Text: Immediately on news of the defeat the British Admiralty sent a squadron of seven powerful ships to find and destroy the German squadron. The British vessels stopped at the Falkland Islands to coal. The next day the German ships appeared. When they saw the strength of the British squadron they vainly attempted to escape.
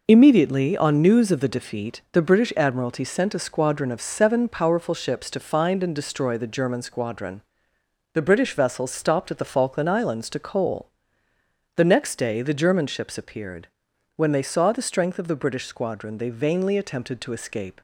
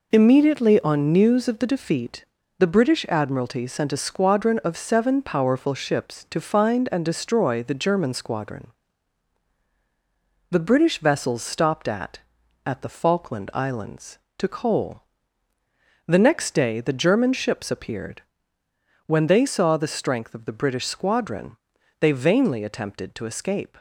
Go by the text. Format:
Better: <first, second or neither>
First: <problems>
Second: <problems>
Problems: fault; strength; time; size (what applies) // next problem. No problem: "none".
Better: first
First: none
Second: pauses between "defeat" and "the"; slight; at 2.2 s; 0.34 s long // says "at" twice; at 12.6 s // pauses between "squadron" and "they"; at 21.5 s; 0.44 s long